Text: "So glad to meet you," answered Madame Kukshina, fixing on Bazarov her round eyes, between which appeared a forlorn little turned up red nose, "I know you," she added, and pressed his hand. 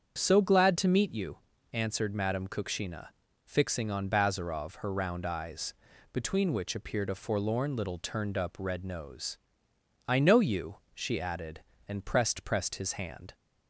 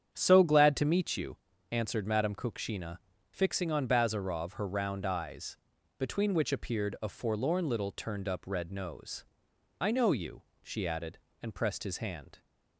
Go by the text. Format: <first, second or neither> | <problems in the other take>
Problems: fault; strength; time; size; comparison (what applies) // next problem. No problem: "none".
second | starts louder than the rest; strong; until 1.1 s; 7.5 dB; strong in the second // says "pressed" twice; at 12.4 s